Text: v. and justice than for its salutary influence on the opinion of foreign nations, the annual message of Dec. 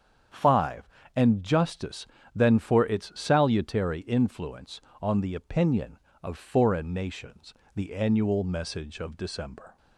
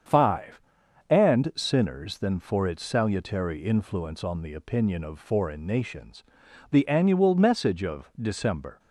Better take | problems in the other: first | starts louder than the rest; strong; until 1.6 s; 7.5 dB; strong in the first // says "sinners" for "justice"; at 1.5 s

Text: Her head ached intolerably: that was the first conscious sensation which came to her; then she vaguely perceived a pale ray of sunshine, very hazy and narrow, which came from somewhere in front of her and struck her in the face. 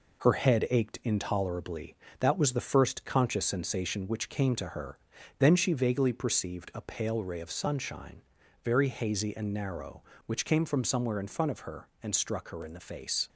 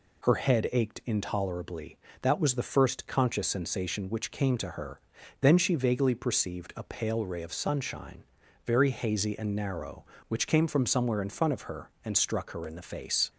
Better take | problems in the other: second | gets quieter; noticeable; throughout; 4.5 dB

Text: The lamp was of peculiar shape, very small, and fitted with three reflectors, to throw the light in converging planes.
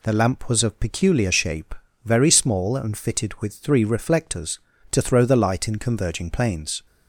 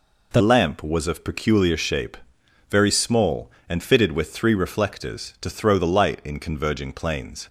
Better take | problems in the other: first | changes voice at "lamp"; from 0.4 s on; 7.0 s long

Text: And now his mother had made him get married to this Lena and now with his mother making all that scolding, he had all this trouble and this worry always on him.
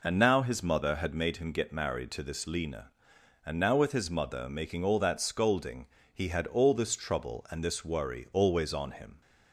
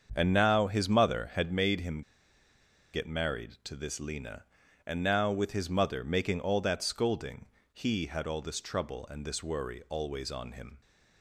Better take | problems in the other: first | starts louder than the rest; until 1.1 s; 7 dB // pauses between "him" and "get"; noticeable; at 2.0 s; 0.92 s long

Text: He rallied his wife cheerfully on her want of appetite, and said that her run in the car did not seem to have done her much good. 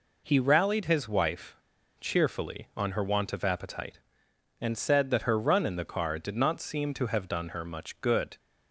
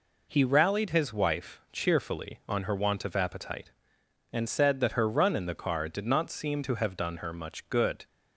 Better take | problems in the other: second | pauses between "wife" and "cheerfully"; noticeable; at 1.5 s; 0.47 s long

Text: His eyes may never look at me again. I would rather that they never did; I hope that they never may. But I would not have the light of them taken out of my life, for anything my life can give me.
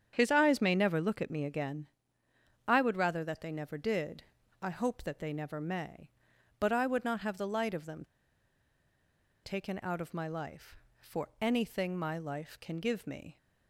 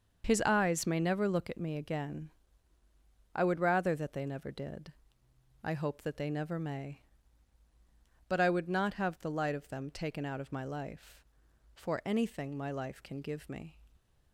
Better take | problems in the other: second | starts louder than the rest; strong; until 1.1 s; 8 dB; also in the second // pauses between "them" and "taken"; strong; at 8.0 s; 1.3 s long

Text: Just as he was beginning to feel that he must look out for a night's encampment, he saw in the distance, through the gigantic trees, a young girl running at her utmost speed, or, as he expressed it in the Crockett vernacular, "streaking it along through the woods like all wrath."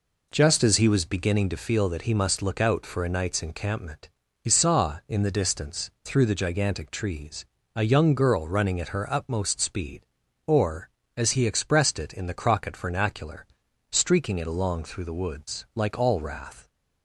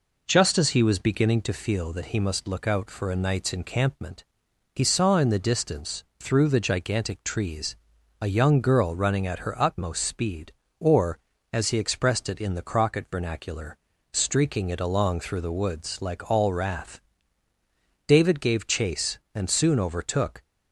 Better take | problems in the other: first | goes on to say "David gave chase and soon overtook"; strong; from 18.0 s on; 2.3 s long

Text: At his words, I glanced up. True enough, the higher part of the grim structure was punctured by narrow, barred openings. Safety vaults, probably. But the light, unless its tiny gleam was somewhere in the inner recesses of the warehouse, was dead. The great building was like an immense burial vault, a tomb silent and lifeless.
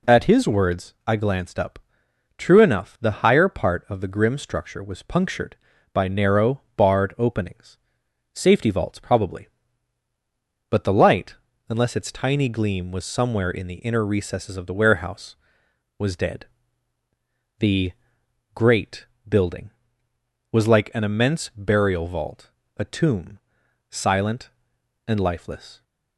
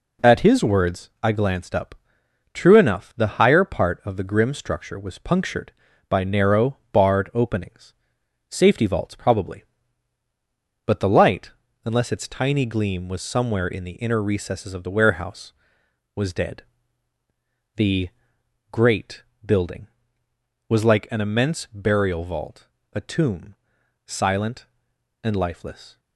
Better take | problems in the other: first | gets quieter; noticeable; throughout; 5.5 dB // pauses between "The" and "great"; noticeable; at 18.0 s; 0.62 s long; noticeable in the first // pauses between "great" and "building"; slight; at 19.2 s; 0.24 s long; slight in the first // pauses between "tomb" and "silent"; noticeable; at 23.5 s; 0.50 s long; noticeable in the first

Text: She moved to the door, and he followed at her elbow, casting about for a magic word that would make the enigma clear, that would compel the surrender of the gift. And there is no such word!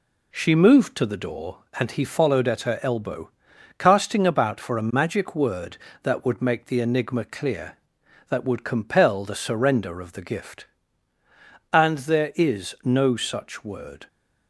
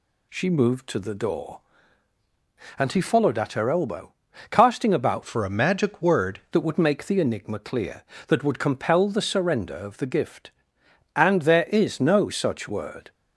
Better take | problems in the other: first | changes voice from "for" to "word"; from 5.2 to 6.4 s; 1.2 s long

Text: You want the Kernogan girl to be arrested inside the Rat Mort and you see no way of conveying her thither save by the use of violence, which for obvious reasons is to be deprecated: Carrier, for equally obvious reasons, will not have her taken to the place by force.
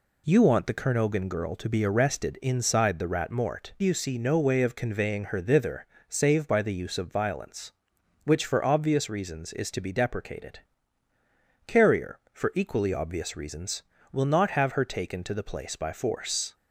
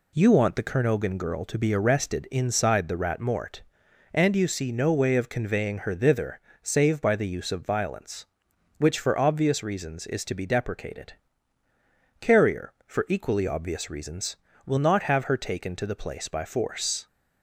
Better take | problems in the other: second | skips "and"; at 3.7 s // pauses between "thither" and "save"; slight; at 5.8 s; 0.24 s long; slight in the second

